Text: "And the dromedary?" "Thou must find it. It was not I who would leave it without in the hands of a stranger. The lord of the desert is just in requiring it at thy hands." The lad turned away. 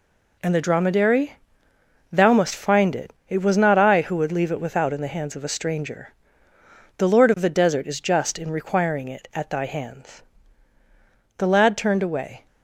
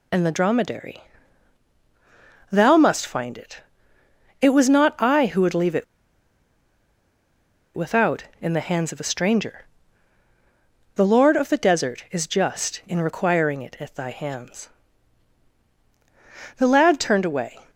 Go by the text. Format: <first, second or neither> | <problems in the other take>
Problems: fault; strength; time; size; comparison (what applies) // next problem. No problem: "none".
first | pauses between "it" and "without"; strong; at 5.8 s; 1.9 s long